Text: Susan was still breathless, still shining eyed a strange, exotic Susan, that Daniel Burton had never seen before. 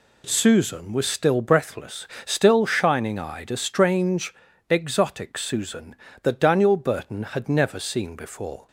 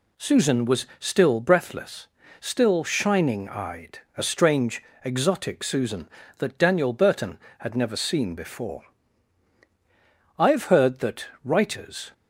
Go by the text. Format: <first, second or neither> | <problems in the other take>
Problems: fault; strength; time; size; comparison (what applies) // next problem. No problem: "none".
first | pauses between "eyed" and "a"; slight; at 3.9 s; 0.18 s long // goes on to say "I've heard that writers"; strong; from 10.3 s on; 1.7 s long